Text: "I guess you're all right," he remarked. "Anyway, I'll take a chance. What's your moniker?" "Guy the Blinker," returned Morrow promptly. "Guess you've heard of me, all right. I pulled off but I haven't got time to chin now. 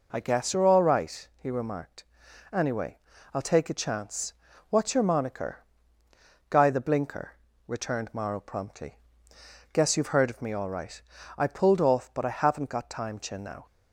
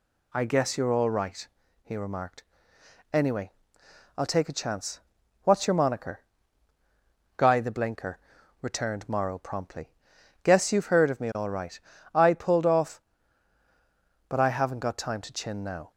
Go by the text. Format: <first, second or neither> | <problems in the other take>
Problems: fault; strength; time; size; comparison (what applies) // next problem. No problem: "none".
second | skips "to"; at 13.1 s